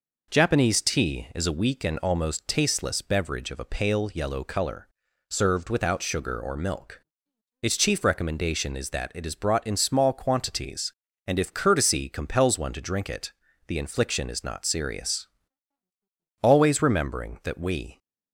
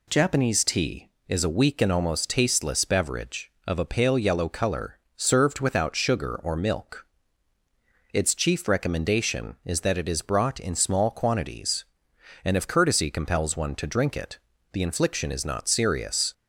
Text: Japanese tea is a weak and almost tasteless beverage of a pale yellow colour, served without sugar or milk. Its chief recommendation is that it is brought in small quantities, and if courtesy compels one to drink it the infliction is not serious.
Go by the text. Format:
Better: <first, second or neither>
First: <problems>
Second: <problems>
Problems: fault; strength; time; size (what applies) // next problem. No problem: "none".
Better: second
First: pauses between "it" and "the"; slight; at 13.3 s; 0.36 s long // goes on to say "Always remembering that we"; from 16.4 s on; 1.5 s long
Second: pauses between "it" and "the"; slight; at 14.3 s; 0.34 s long